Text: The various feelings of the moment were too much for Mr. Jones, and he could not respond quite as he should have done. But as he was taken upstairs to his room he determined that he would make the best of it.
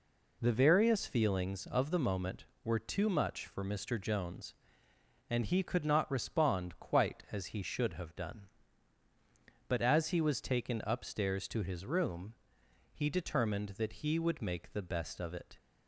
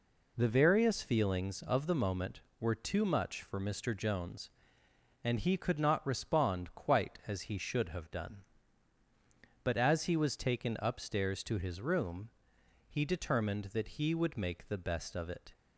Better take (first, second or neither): neither